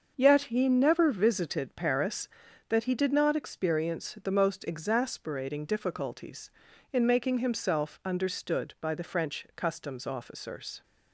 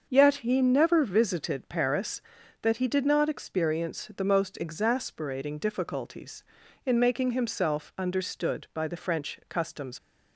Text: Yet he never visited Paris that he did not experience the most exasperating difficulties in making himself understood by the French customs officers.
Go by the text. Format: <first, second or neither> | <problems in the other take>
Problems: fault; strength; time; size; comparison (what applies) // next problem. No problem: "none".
first | starts louder than the rest; until 1.1 s; 6.5 dB; also in the first // stops before "officers"; at 9.9 s